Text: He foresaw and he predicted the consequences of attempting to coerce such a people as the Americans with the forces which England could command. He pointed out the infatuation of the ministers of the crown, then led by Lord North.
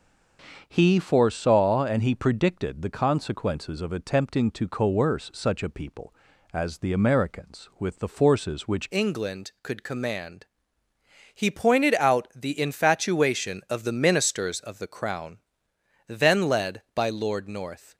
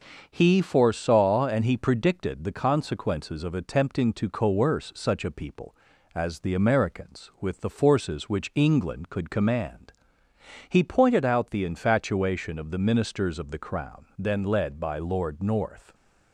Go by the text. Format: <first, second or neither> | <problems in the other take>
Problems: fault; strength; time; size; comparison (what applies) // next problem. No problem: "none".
second | starts louder than the rest; until 1.6 s; 6.5 dB; also in the second // changes voice at "England"; from 8.9 s on; 9.0 s long